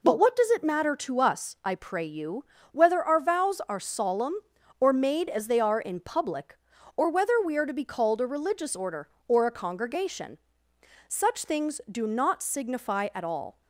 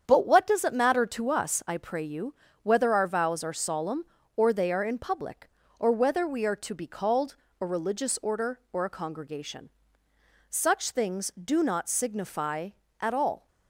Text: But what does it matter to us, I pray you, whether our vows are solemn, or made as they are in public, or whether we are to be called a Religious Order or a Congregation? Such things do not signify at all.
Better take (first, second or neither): first